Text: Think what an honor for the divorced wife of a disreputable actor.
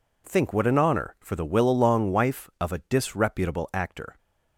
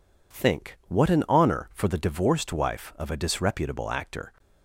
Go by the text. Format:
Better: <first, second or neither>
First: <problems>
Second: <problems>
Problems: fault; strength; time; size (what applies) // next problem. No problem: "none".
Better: second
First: says "willalong" for "divorced"; at 1.4 s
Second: none